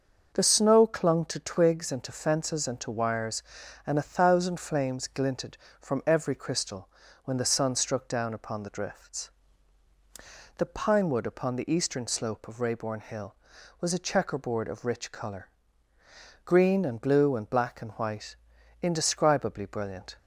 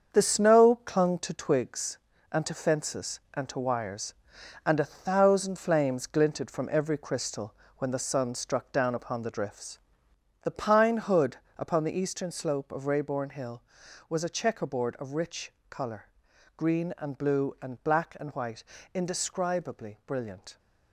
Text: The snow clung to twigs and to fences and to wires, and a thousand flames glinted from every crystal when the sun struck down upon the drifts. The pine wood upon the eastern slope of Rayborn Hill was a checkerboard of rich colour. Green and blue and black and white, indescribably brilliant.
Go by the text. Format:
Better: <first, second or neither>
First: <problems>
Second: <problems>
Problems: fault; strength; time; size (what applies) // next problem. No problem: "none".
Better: first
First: starts louder than the rest; until 1.3 s; 6.5 dB // pauses between "crystal" and "when"; slight; at 6.8 s; 0.34 s long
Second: starts louder than the rest; strong; until 1.2 s; 7 dB // pauses between "crystal" and "when"; slight; at 7.5 s; 0.24 s long // says "hood" for "wood"; at 10.9 s // pauses between "rich" and "colour"; slight; at 15.5 s; 0.18 s long